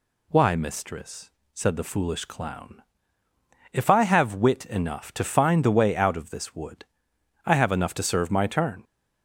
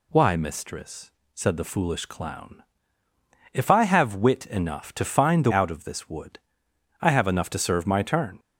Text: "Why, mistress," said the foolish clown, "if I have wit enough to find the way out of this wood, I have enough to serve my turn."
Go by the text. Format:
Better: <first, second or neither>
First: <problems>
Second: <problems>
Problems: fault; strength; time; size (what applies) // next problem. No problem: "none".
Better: first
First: none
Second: skips "way"; at 5.5 s